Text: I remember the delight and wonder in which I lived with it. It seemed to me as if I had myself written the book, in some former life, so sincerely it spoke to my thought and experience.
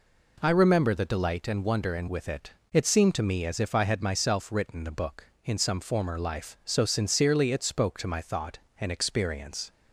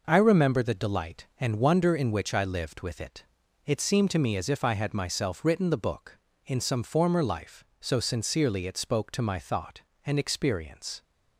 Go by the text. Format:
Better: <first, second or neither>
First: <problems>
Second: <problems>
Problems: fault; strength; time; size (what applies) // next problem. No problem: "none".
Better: second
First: skips "which I lived"; at 2.0 s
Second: none